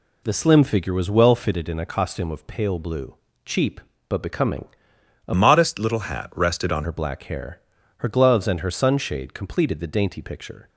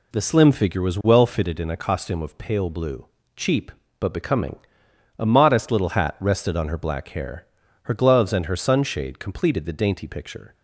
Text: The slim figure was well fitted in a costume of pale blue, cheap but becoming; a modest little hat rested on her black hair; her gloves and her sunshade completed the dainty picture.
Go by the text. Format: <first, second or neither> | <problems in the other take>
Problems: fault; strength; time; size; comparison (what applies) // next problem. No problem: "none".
second | changes voice from "modest" to "on"; from 5.3 to 6.8 s; 1.5 s long